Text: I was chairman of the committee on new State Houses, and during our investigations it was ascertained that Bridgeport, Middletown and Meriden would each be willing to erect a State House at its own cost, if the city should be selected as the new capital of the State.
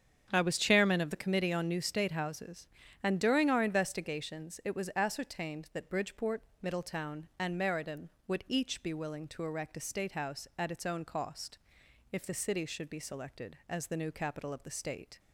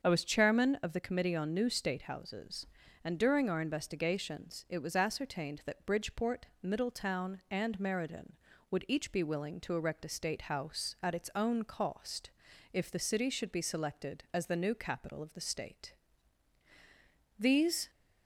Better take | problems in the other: first | starts louder than the rest; until 1.0 s; 6.5 dB; strong in the first // goes on to say "These"; from 17.3 s on; 0.50 s long

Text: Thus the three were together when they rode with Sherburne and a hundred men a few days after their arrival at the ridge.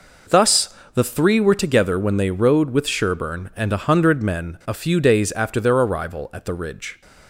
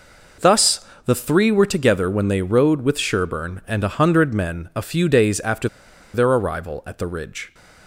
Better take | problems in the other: first | pauses between "Thus" and "the"; slight; at 0.8 s; 0.20 s long; slight in the first // pauses between "after" and "their"; noticeable; at 5.6 s; 0.46 s long

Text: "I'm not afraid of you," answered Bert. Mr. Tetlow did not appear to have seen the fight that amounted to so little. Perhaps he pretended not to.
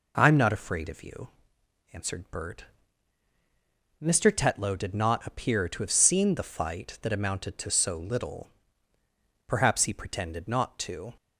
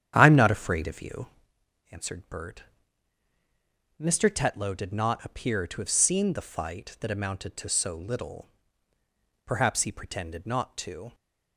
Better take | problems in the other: first | starts louder than the rest; strong; until 1.5 s; 10 dB

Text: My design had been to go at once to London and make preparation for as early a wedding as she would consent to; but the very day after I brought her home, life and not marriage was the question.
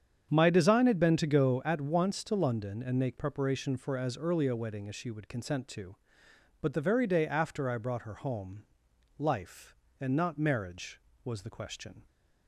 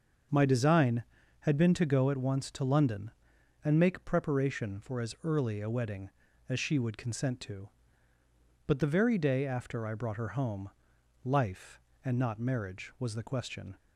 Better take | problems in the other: neither | starts louder than the rest; the same in both

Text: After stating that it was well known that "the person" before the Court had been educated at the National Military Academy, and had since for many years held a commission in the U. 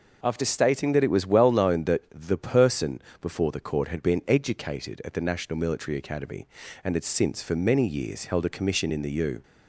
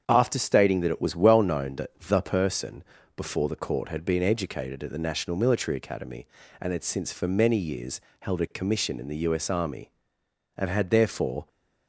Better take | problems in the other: first | starts louder than the rest; strong; until 1.0 s; 7.5 dB // pauses between "person" and "before"; slight; at 2.8 s; 0.34 s long; slight in the first // pauses between "years" and "held"; slight; at 8.0 s; 0.18 s long // goes on to say "S Army and had therefore"; strong; from 9.3 s on; 2.1 s long

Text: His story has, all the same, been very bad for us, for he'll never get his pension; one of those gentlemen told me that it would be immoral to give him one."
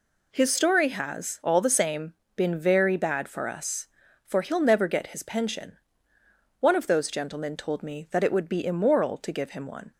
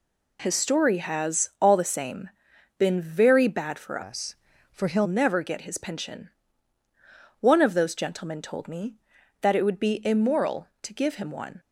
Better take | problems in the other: first | changes voice from "us" to "he'll"; from 4.0 to 5.0 s; 1.0 s long

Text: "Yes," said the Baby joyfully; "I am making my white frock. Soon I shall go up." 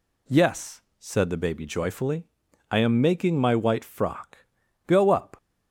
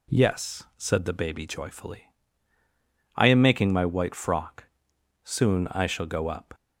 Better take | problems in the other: second | skips "Soon I shall"; at 4.6 s

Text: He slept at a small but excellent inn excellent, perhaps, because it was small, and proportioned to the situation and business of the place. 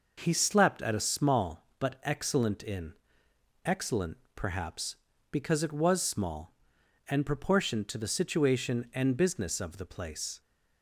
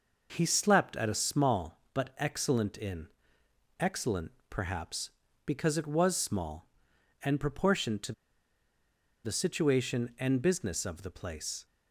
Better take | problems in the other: first | pauses between "inn" and "excellent"; noticeable; at 3.0 s; 0.72 s long; noticeable in the first // pauses between "to" and "the"; at 8.1 s; 1.1 s long

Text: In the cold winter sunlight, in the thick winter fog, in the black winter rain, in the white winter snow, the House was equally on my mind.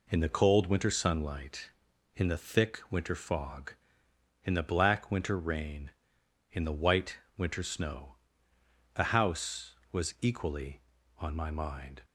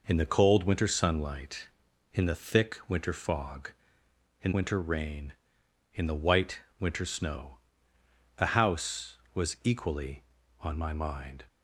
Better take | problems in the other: first | skips "the black"; at 4.5 s // pauses between "white" and "winter"; slight; at 6.5 s; 0.20 s long; slight in the first

